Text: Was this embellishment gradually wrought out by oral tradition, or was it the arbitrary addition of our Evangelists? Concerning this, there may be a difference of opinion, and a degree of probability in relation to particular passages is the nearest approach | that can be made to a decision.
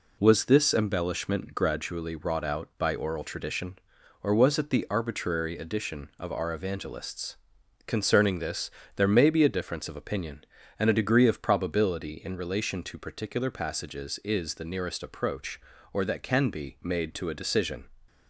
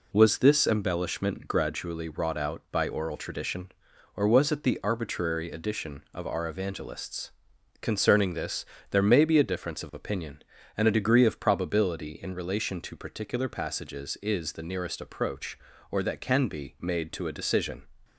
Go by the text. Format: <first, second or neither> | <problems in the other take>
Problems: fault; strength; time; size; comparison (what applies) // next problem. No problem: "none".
neither | none